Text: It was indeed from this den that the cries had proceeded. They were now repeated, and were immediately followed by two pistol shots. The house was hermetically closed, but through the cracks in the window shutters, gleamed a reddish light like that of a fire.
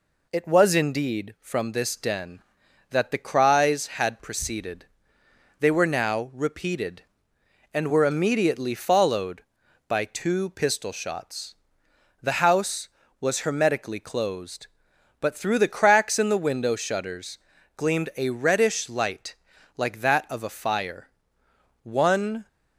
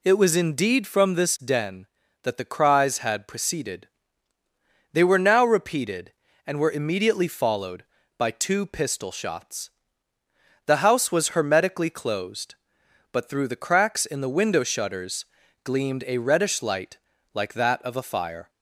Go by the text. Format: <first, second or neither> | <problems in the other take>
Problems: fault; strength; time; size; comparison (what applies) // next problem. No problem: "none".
second | pauses between "light" and "like"; at 19.3 s; 0.42 s long; slight in the second // goes on to say "One"; noticeable; from 21.8 s on; 0.64 s long